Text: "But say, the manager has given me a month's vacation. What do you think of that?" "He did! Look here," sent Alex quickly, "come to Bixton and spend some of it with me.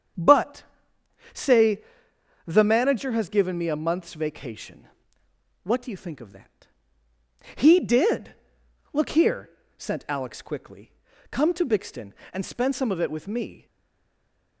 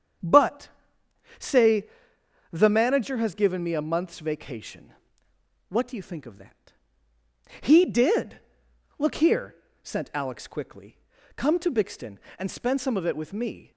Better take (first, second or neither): second